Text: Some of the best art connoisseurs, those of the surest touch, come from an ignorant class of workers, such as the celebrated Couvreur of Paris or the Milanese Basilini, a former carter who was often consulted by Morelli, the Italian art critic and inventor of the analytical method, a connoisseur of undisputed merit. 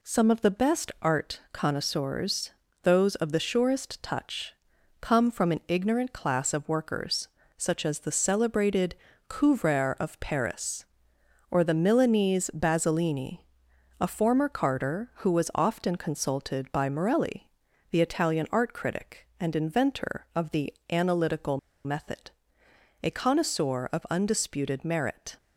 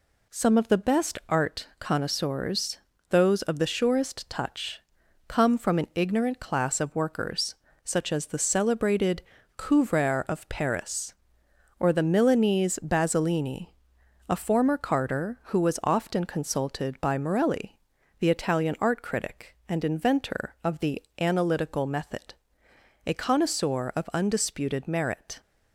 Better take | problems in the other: second | pauses between "celebrated" and "Couvreur"; slight; at 8.9 s; 0.32 s long; slight in the second // pauses between "the" and "analytical"; slight; at 20.7 s; 0.20 s long; slight in the second // pauses between "analytical" and "method"; slight; at 21.5 s; 0.27 s long

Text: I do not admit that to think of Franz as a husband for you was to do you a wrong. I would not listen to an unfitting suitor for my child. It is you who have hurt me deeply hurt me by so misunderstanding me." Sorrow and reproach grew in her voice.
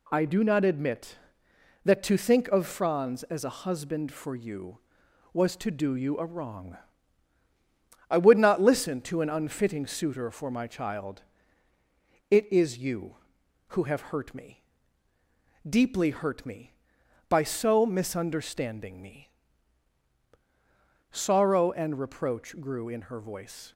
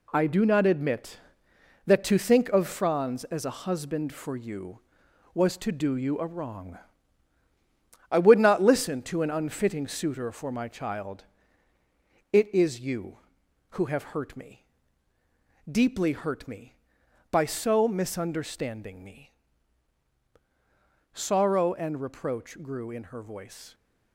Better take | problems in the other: first | gets quieter; strong; throughout; 7.5 dB // pauses between "me" and "deeply"; at 14.6 s; 1.0 s long; also in the first

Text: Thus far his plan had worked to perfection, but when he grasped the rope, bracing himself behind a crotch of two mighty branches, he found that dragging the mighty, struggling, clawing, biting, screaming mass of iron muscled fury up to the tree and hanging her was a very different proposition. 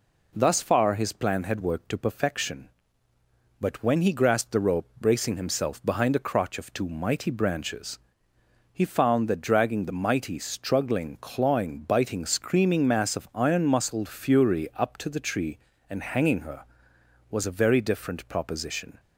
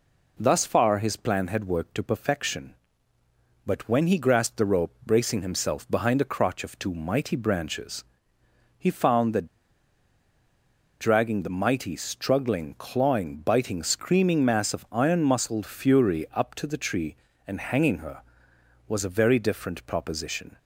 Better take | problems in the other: first | pauses between "that" and "dragging"; strong; at 9.4 s; 1.5 s long

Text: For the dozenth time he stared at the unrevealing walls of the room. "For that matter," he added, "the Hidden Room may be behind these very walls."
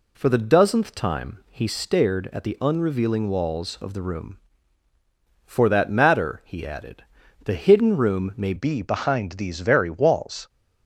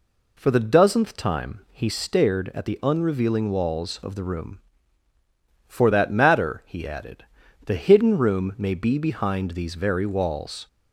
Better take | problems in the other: second | changes voice at "be"; from 8.5 s on; 1.9 s long

